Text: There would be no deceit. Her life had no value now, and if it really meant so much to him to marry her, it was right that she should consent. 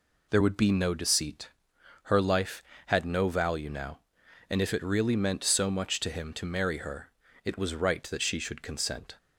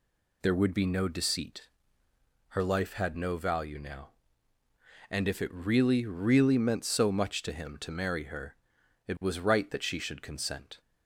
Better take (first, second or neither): first